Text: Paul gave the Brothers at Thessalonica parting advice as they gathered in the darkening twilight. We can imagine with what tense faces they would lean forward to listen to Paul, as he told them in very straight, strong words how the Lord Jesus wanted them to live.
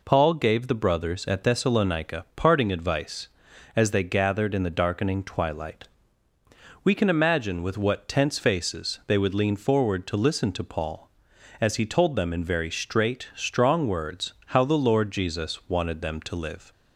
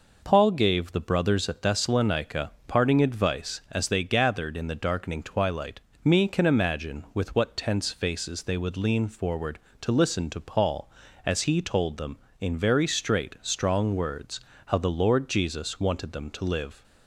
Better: first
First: none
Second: pauses between "Thessalonica" and "parting"; slight; at 2.5 s; 0.16 s long // says "Me" for "We"; at 6.0 s // pauses between "words" and "how"; slight; at 14.4 s; 0.26 s long

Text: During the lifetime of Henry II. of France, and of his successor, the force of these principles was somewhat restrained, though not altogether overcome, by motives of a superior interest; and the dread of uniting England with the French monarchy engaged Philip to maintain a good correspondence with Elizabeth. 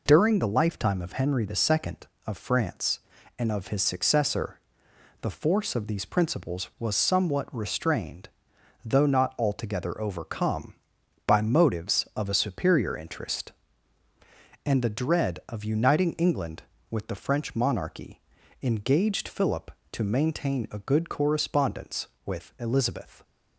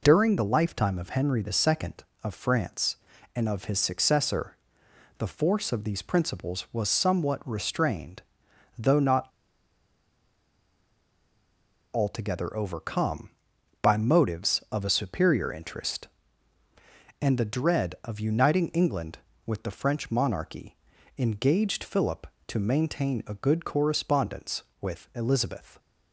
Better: first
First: pauses between "monarchy" and "engaged"; at 18.2 s; 0.42 s long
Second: pauses between "not" and "altogether"; strong; at 9.2 s; 2.6 s long // pauses between "monarchy" and "engaged"; at 20.7 s; 0.42 s long

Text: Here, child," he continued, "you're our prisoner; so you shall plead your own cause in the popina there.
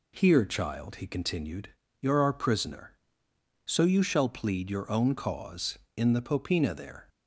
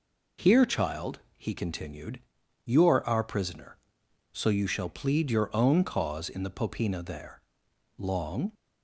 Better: first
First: none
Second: goes on to say "Long"; from 7.9 s on; 0.56 s long

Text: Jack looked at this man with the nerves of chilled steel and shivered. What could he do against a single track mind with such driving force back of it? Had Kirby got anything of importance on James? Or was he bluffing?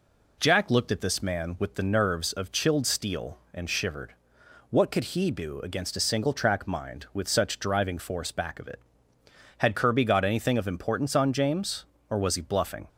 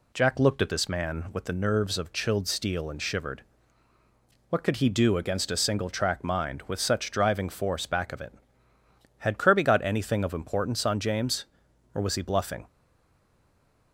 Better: first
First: none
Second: stays silent after the last word; noticeable; from 12.6 s on; 1.3 s long

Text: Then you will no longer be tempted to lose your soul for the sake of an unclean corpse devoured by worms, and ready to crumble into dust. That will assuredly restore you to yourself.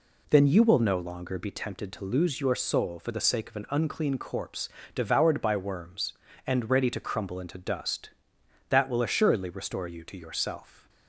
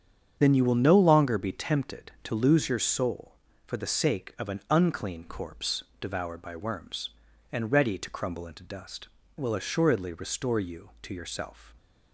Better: first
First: pauses between "corpse" and "devoured"; slight; at 4.6 s; 0.26 s long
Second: starts louder than the rest; strong; until 1.4 s; 8 dB // pauses between "corpse" and "devoured"; slight; at 5.8 s; 0.16 s long // skips "That"; at 9.2 s

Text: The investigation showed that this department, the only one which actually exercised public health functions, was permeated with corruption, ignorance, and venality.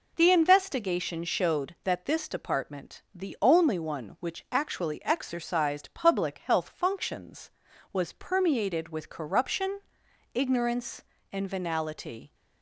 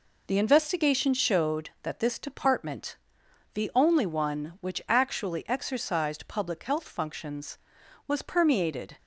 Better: first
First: none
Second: stops before "with corruption ignorance and venality"; at 8.9 s

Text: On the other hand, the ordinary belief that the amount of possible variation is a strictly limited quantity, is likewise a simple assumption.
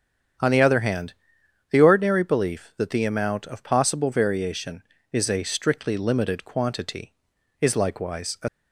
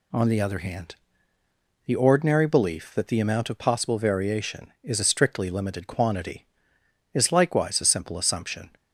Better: second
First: starts louder than the rest; strong; until 1.9 s; 8.5 dB // stops before "simple assumption"; at 8.4 s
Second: none

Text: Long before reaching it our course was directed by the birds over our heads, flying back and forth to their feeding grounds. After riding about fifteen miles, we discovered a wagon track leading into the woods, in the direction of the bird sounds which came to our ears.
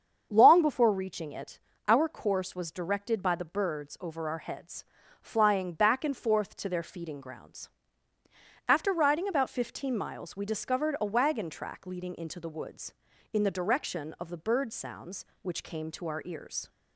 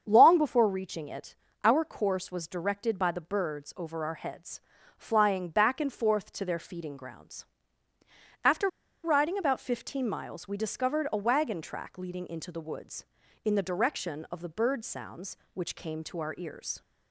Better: first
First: starts louder than the rest; strong; until 1.3 s; 7 dB // pauses between "it" and "our"; slight; at 1.5 s; 0.28 s long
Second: starts louder than the rest; strong; until 1.0 s; 7 dB // pauses between "it" and "our"; slight; at 1.3 s; 0.28 s long // pauses between "After" and "riding"; at 8.6 s; 0.36 s long

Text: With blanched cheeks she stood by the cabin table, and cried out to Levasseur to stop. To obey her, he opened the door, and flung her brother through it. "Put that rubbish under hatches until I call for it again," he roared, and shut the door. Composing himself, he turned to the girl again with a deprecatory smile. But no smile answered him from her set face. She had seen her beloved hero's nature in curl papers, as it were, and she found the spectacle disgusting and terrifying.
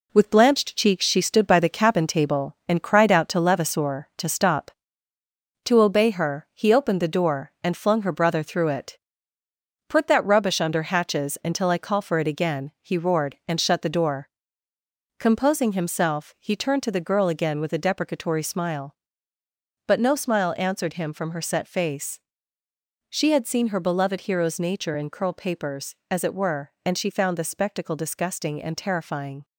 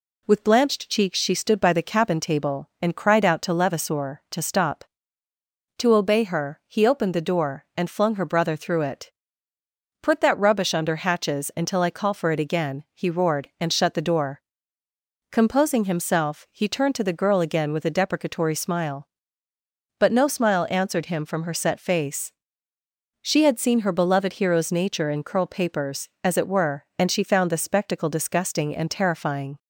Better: second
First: gets quieter; noticeable; throughout; 6 dB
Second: none

